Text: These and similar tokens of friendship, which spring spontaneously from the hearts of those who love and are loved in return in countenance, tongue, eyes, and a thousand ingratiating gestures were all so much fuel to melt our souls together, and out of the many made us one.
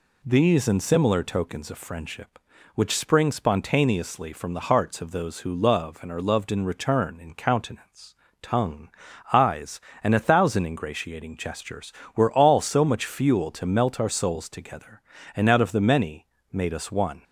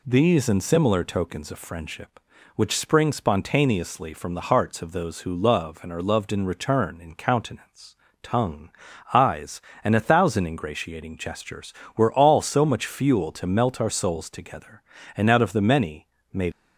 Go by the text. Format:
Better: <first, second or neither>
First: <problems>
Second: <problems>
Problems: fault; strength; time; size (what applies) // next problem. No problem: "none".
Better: first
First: pauses between "many" and "made"; slight; at 16.2 s; 0.28 s long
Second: pauses between "many" and "made"; slight; at 16.0 s; 0.28 s long // stops before "us one"; at 16.5 s